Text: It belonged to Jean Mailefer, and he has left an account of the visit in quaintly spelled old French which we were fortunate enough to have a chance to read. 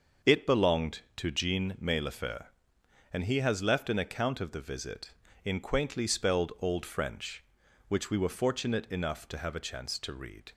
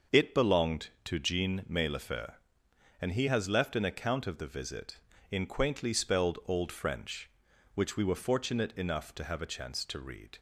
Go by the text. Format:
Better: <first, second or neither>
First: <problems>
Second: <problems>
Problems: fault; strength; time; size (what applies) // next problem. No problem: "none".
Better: neither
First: starts louder than the rest; until 1.4 s; 6.5 dB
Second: starts louder than the rest; until 1.2 s; 6.5 dB